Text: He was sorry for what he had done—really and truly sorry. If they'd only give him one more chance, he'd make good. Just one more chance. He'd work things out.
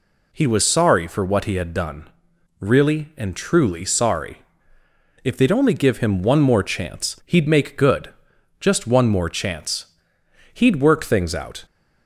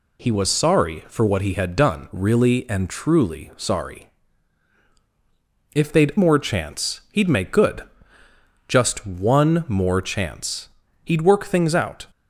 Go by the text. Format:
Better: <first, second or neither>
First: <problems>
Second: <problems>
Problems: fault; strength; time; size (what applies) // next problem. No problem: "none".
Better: first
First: none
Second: skips "only give him one"; at 6.1 s